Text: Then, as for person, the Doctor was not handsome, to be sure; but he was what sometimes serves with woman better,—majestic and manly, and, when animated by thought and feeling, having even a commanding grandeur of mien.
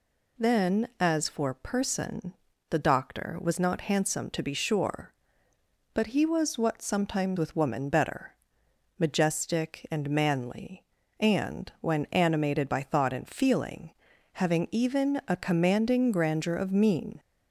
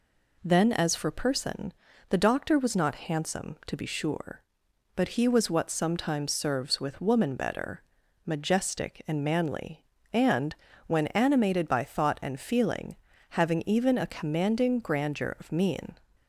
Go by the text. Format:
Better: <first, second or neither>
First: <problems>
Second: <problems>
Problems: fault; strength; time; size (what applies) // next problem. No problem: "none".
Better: second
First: skips "serves"; at 7.3 s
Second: none